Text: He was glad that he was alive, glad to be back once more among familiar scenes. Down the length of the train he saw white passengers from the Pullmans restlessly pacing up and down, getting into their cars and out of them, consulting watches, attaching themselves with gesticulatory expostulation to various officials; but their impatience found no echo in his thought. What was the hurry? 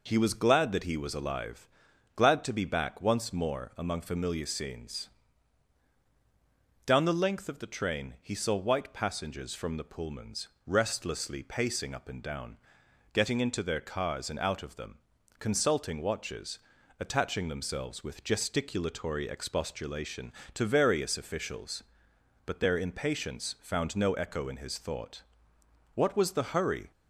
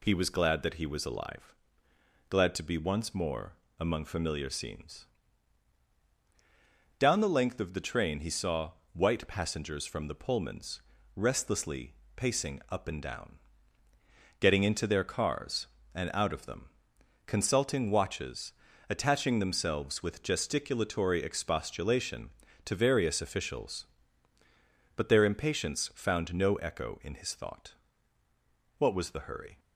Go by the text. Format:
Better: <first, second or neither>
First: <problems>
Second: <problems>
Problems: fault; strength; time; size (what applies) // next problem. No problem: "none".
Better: first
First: pauses between "Pullmans" and "restlessly"; slight; at 10.4 s; 0.18 s long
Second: skips "back"; at 2.7 s // pauses between "more" and "among"; slight; at 3.5 s; 0.26 s long // pauses between "saw" and "white"; slight; at 8.7 s; 0.22 s long // pauses between "Pullmans" and "restlessly"; slight; at 10.8 s; 0.34 s long // pauses between "restlessly" and "pacing"; slight; at 11.9 s; 0.24 s long